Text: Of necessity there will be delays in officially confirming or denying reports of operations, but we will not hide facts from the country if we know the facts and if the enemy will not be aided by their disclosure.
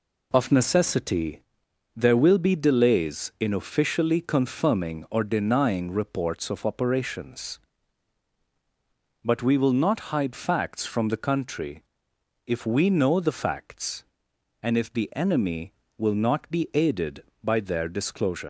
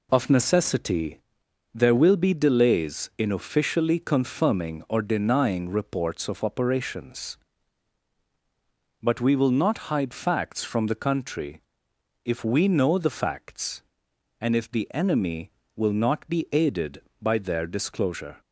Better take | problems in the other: second | pauses between "necessity" and "there"; noticeable; at 1.4 s; 0.52 s long; noticeable in the second // pauses between "country" and "if"; noticeable; at 11.8 s; 0.64 s long; noticeable in the second // leaves "disclosure" unfinished; at 18.4 s; 135 ms

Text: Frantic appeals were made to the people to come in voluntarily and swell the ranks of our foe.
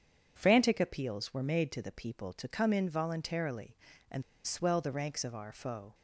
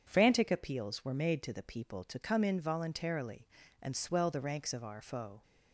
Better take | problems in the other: second | starts louder than the rest; strong; until 1.3 s; 7.5 dB // pauses between "and" and "swell"; slight; at 4.2 s; 0.21 s long

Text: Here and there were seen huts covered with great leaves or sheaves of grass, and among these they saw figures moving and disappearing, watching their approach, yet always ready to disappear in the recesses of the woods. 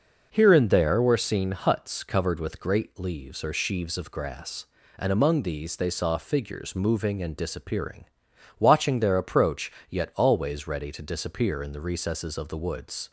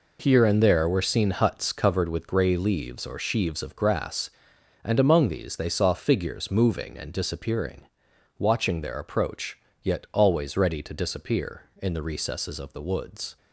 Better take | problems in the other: first | says "grey" for "great"; at 2.2 s

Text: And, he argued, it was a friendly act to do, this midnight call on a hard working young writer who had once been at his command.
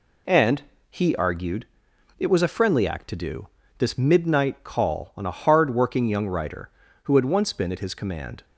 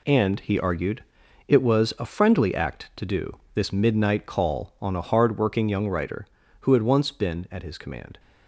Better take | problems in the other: first | gets quieter; strong; throughout; 8.5 dB

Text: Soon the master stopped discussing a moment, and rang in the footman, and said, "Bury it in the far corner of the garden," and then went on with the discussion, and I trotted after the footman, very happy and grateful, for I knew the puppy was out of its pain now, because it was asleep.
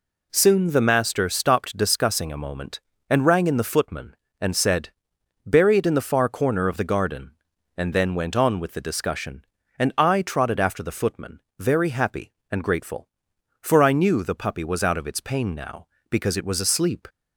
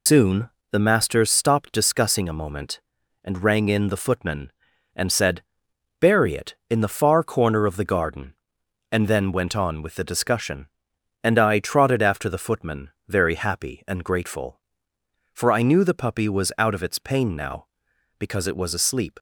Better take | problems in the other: first | loses the start of "Soon"; at 0.0 s; 105 ms // pauses between "Soon" and "the"; slight; at 0.5 s; 0.22 s long

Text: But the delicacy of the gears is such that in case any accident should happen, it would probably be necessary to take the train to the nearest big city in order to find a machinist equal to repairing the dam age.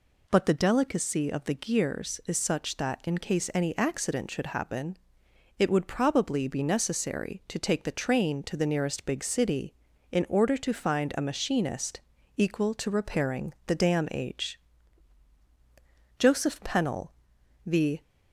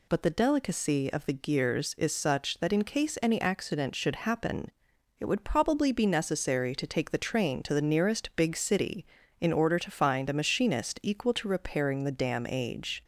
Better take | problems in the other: second | pauses between "machinist" and "equal"; slight; at 12.0 s; 0.34 s long // goes on to say "Joseph Pennell the"; strong; from 16.1 s on; 1.8 s long

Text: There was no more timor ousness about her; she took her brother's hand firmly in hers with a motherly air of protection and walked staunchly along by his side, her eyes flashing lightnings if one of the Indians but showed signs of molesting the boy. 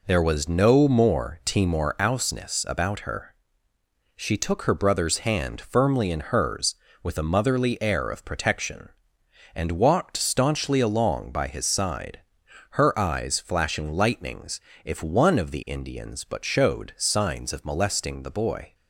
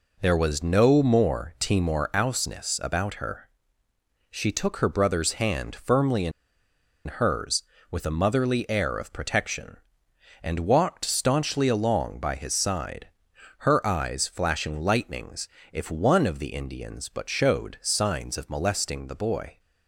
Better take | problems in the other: first | pauses between "in" and "hers"; noticeable; at 6.3 s; 0.75 s long // pauses between "lightnings" and "if"; slight; at 15.4 s; 0.24 s long; slight in the first

